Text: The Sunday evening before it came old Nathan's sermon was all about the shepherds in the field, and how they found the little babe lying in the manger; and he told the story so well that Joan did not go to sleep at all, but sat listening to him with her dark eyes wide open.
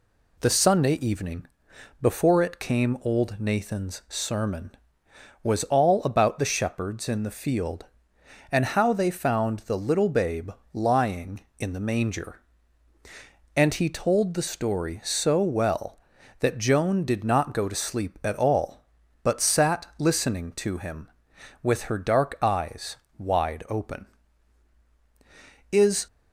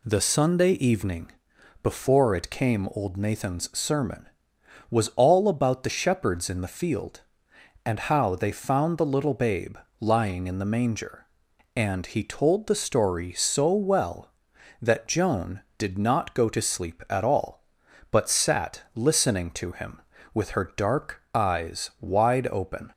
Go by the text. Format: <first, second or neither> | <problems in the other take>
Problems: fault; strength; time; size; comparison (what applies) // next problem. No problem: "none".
second | pauses between "evening" and "before"; noticeable; at 1.4 s; 0.54 s long; noticeable in the second // pauses between "babe" and "lying"; slight; at 10.5 s; 0.20 s long; slight in the second // pauses between "eyes" and "wide"; slight; at 22.9 s; 0.22 s long // goes on to say "Is"; slight; from 25.7 s on; 0.34 s long